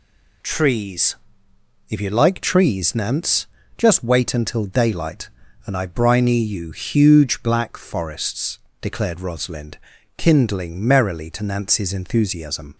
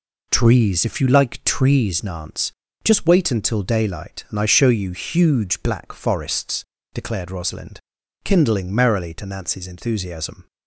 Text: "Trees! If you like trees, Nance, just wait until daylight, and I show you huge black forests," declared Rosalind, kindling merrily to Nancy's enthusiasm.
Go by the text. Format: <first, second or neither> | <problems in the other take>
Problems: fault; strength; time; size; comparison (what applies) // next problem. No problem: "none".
second | says "briny" for "show"; at 5.8 s